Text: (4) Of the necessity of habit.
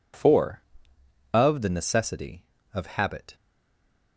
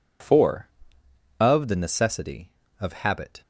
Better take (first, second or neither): second